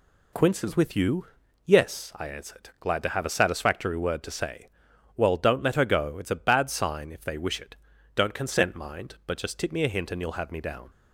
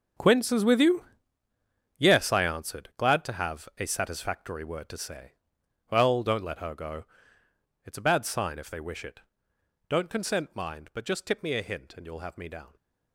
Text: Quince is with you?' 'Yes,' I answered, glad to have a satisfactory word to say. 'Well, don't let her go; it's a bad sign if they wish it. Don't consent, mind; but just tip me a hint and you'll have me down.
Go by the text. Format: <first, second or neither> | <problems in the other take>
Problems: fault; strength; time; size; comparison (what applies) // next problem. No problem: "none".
first | gets quieter; strong; throughout; 14 dB